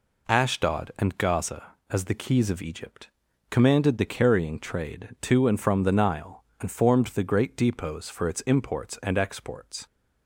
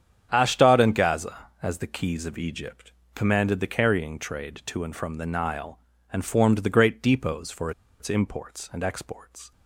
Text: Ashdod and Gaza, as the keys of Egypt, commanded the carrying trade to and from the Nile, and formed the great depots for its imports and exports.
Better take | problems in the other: first | starts louder than the rest; strong; until 1.3 s; 8.5 dB // pauses between "for" and "its"; slight; at 7.7 s; 0.29 s long

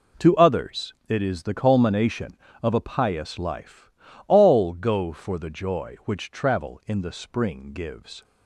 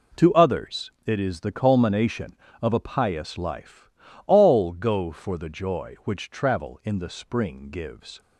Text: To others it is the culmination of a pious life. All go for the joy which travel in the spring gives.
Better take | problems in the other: neither | pauses between "others" and "it"; slight; the same in both

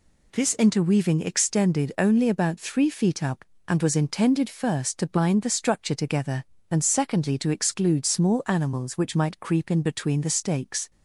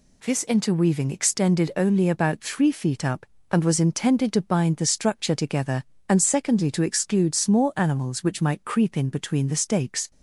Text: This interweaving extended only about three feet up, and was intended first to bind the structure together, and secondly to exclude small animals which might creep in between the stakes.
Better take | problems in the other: first | skips "first"; at 4.3 s

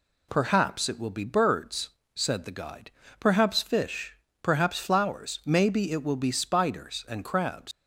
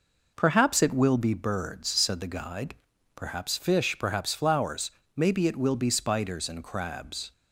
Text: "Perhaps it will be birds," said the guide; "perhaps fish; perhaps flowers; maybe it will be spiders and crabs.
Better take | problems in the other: second | leaves "crabs" unfinished; at 7.7 s; 105 ms

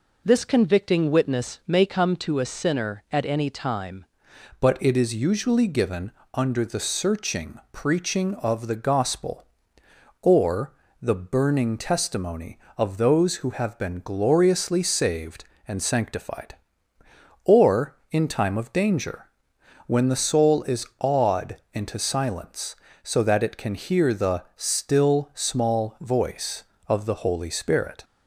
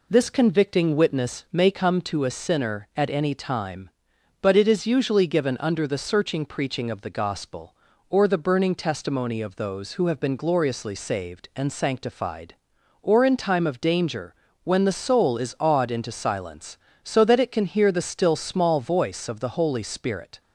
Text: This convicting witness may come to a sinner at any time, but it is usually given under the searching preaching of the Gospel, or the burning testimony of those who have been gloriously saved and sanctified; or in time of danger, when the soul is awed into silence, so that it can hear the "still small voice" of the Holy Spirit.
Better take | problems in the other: second | changes voice at "but"; from 4.5 s on; 23.5 s long // pauses between "given" and "under"; slight; at 6.1 s; 0.20 s long // pauses between "or" and "the"; slight; at 10.7 s; 0.28 s long // pauses between "awed" and "into"; slight; at 21.5 s; 0.16 s long

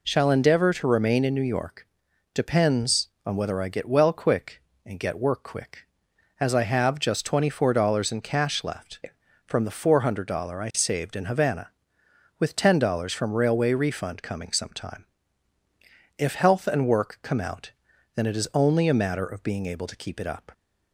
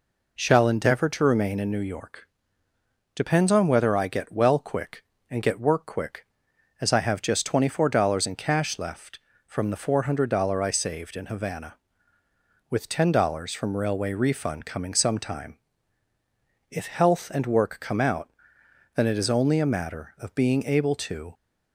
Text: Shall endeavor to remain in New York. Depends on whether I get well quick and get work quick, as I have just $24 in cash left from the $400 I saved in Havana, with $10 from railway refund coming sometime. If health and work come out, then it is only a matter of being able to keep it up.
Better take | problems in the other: first | stops before "keep it up"; at 21.3 s

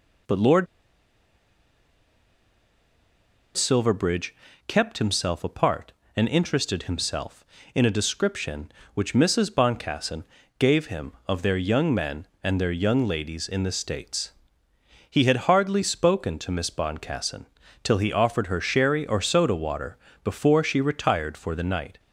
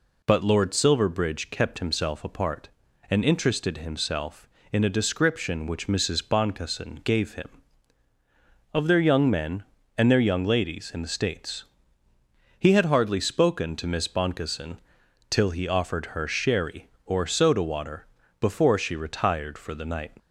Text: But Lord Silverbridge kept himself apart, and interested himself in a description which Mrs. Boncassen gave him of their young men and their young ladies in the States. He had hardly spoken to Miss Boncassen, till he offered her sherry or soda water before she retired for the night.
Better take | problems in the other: second | pauses between "Lord" and "Silverbridge"; strong; at 0.6 s; 2.9 s long // pauses between "Silverbridge" and "kept"; slight; at 4.3 s; 0.32 s long // pauses between "Boncassen" and "gave"; slight; at 10.2 s; 0.36 s long // pauses between "water" and "before"; slight; at 19.9 s; 0.26 s long; slight in the second

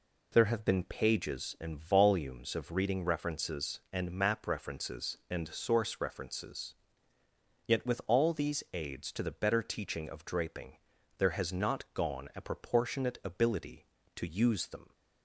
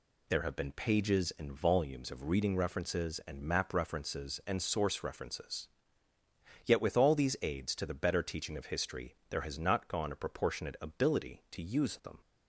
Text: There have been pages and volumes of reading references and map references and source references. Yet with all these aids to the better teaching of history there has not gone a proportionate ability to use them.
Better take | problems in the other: second | says "draping" for "history"; at 10.2 s

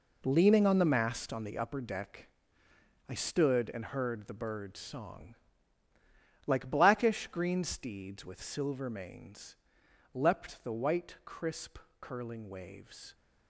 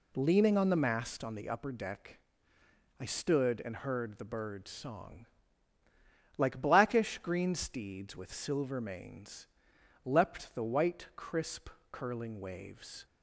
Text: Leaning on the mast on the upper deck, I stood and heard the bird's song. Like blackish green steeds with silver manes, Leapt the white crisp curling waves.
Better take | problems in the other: second | gets quieter; strong; throughout; 10.5 dB // pauses between "crisp" and "curling"; slight; at 11.7 s; 0.24 s long; slight in the second

